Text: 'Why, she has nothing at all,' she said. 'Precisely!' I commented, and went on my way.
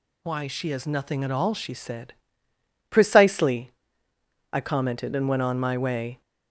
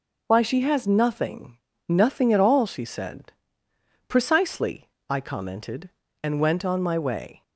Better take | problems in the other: first | says "nothing" twice; at 1.8 s

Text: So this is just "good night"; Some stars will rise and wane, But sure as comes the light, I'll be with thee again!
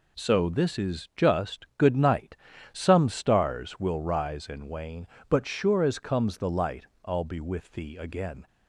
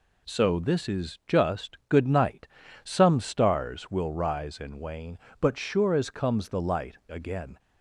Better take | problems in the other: first | skips "I'll be with thee"; at 7.0 s

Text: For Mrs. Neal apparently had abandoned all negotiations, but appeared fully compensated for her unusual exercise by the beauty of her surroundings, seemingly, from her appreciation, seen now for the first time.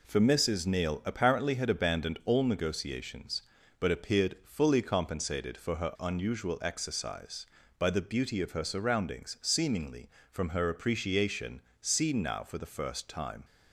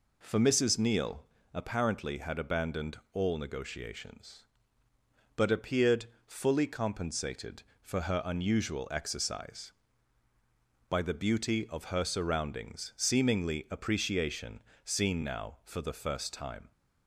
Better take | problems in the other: first | pauses between "Neal" and "apparently"; slight; at 1.2 s; 0.28 s long // pauses between "appeared" and "fully"; slight; at 6.0 s; 0.20 s long // skips "from her"; at 13.6 s

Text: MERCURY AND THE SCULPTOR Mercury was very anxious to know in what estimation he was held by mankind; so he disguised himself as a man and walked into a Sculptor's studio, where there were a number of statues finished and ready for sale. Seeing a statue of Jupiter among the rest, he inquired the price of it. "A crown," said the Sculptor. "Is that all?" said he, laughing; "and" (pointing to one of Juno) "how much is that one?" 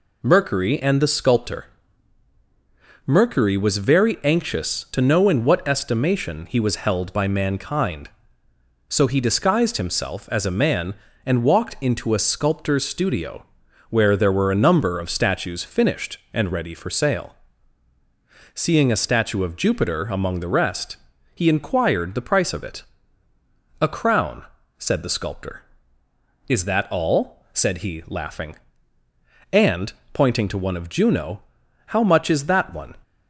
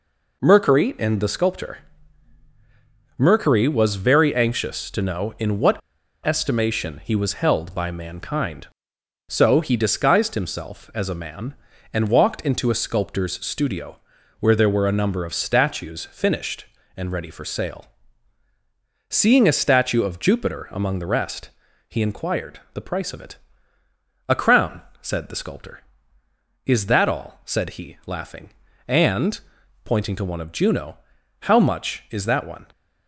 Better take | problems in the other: first | pauses between "SCULPTOR" and "Mercury"; strong; at 1.7 s; 1.3 s long; strong in the first // pauses between "what" and "estimation"; at 5.8 s; 0.43 s long

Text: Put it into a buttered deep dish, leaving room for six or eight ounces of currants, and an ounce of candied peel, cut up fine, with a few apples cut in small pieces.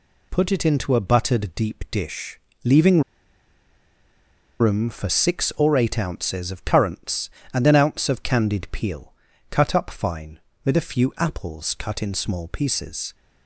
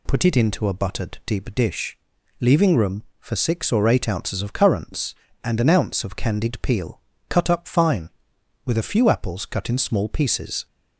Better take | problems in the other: second | pauses between "leaving" and "room"; strong; at 3.0 s; 1.5 s long

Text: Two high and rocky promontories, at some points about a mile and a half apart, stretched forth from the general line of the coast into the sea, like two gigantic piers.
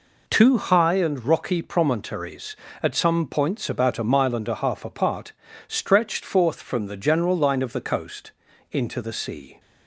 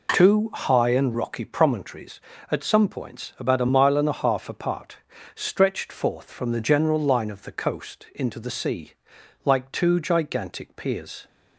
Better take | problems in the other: second | pauses between "coast" and "into"; at 8.3 s; 0.40 s long // stops before "like two gigantic piers"; at 9.5 s

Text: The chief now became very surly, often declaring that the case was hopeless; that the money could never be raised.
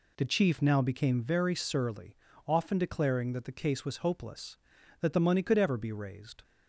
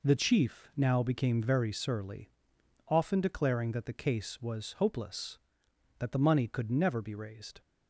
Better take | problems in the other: second | says "ever" for "never"; at 5.5 s

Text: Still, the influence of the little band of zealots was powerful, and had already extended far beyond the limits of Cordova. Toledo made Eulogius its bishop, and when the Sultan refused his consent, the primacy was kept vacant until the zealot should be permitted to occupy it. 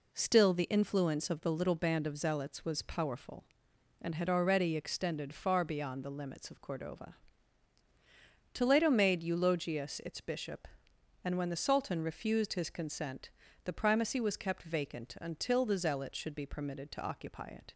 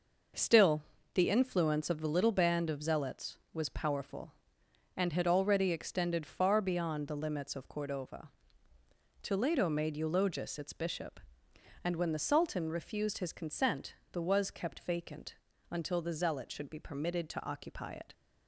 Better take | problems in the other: first | skips "primacy"; at 14.2 s // pauses between "vacant" and "until"; slight; at 15.3 s; 0.36 s long

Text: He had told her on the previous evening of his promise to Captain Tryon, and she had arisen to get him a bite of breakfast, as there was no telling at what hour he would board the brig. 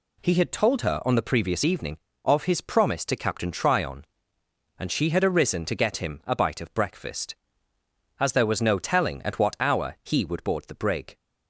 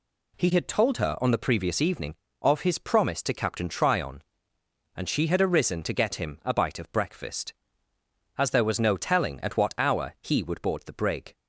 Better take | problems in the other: neither | none

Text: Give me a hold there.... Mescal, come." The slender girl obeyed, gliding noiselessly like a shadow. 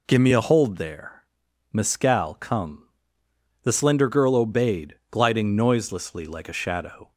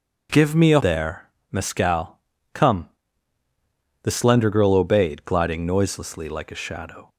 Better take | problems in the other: first | skips "hold"; at 0.7 s

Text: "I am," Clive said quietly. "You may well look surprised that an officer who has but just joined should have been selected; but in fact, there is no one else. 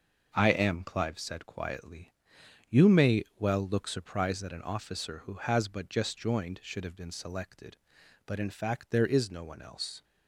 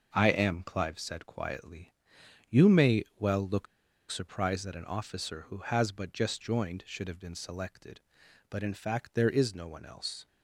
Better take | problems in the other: first | starts louder than the rest; noticeable; until 1.1 s; 6 dB; noticeable in the first // pauses between "look" and "surprised"; at 3.6 s; 0.45 s long

